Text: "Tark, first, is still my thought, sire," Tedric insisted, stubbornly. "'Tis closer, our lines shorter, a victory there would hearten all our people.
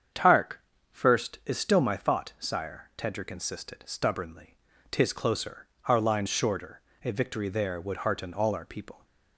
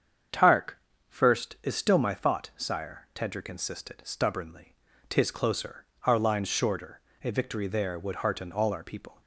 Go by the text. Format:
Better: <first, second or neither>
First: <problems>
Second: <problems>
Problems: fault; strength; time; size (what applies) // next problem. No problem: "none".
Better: neither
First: starts louder than the rest; strong; until 1.5 s; 7.5 dB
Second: starts louder than the rest; strong; until 1.7 s; 7.5 dB